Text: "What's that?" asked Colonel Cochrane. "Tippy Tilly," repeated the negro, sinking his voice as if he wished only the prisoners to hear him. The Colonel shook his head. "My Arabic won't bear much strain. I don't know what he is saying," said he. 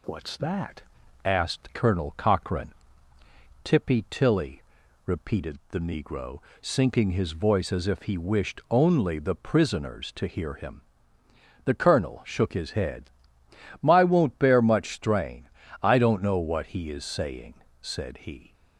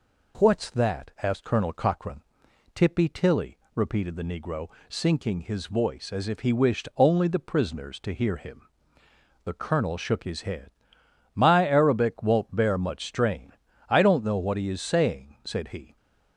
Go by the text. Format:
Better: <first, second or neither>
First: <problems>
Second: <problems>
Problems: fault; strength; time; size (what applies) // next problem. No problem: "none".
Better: second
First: skips "Arabic"; at 14.0 s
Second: none